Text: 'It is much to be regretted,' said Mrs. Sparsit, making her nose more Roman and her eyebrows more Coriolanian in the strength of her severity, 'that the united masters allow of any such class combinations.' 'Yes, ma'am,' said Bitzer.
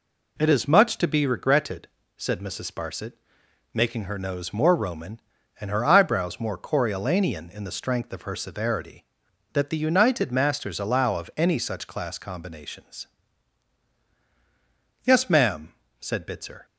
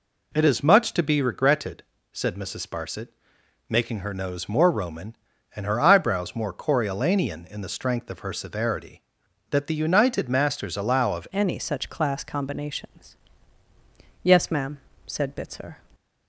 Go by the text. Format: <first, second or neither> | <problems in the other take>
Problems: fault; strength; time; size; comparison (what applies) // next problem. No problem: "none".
first | changes voice at "any"; from 11.3 s on; 4.4 s long